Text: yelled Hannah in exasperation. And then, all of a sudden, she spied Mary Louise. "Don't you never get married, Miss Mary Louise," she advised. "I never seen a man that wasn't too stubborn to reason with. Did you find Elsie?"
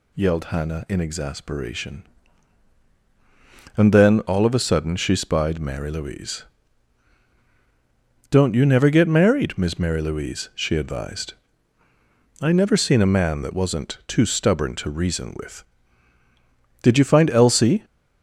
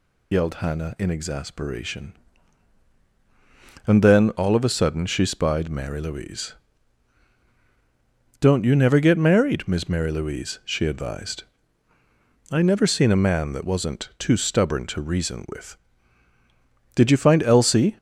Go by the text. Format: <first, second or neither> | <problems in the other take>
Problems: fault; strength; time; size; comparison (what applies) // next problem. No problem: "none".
first | loses the start of "yelled"; at 0.3 s; 80 ms